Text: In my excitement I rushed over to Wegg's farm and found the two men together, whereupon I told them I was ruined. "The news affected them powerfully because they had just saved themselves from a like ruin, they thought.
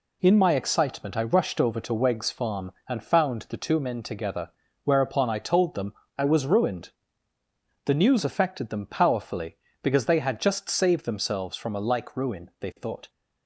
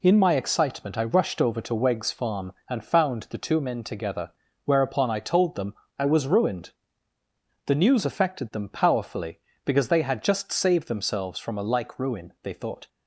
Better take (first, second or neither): neither